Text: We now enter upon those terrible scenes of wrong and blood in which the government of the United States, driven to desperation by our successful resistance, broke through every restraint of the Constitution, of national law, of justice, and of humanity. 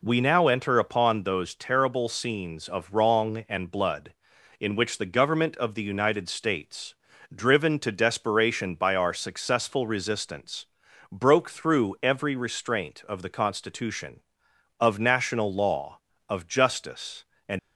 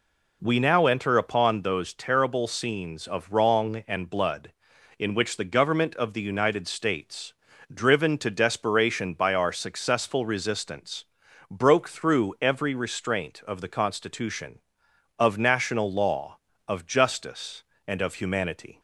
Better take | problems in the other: second | stops before "of humanity"; at 17.5 s

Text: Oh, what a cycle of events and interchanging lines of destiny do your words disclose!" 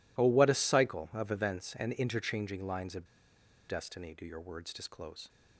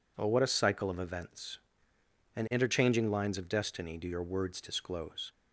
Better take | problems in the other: second | pauses between "of" and "destiny"; noticeable; at 3.0 s; 0.62 s long

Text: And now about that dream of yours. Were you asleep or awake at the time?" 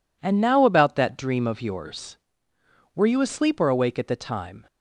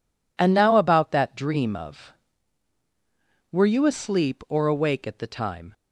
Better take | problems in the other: first | skips "yours"; at 2.8 s

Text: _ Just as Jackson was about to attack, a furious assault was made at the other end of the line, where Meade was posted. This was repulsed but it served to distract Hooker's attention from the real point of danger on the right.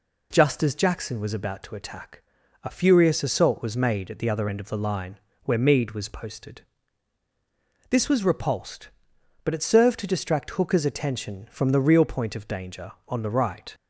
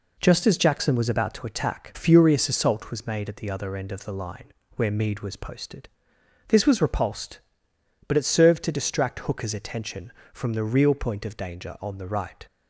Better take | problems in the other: first | skips "a"; at 1.9 s

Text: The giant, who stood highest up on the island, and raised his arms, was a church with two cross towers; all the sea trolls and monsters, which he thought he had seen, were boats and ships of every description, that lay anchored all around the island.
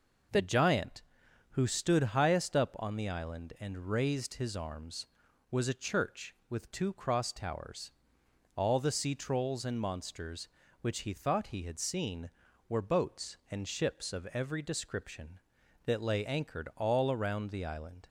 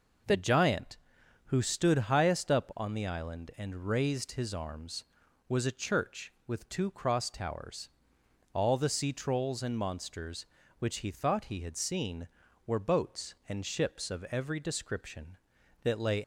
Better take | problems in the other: first | stops before "anchored all around the island"; at 16.2 s

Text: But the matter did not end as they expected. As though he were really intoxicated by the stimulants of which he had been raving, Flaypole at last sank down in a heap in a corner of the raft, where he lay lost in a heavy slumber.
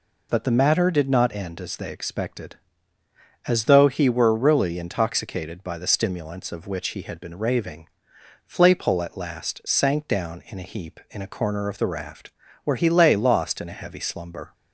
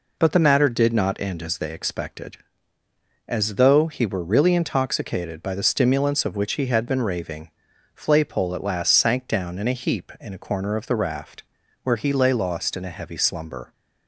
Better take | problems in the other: neither | none

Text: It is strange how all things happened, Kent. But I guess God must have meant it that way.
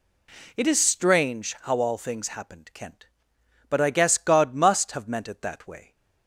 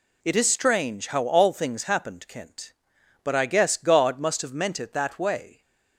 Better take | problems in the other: neither | none

